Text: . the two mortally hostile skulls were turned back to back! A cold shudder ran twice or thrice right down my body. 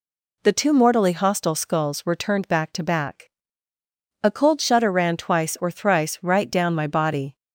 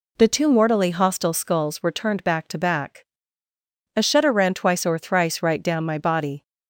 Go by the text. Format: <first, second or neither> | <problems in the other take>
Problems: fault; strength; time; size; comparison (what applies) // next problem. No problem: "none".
first | skips "cold"; at 4.0 s